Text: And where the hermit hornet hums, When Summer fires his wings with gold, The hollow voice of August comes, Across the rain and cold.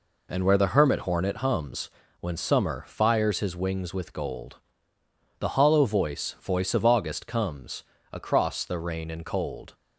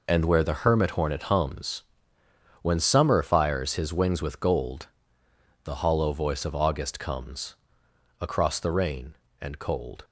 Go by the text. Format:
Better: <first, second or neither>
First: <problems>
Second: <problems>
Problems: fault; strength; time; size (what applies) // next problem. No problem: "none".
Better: second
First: says "voice" twice; at 6.3 s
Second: none